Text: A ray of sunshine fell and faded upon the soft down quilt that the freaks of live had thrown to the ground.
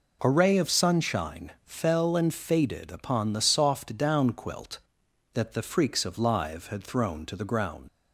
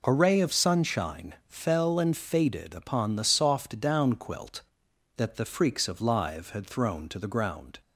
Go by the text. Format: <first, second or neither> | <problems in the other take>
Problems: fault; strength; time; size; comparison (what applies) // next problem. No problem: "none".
second | leaves "ground" unfinished; at 7.8 s; 80 ms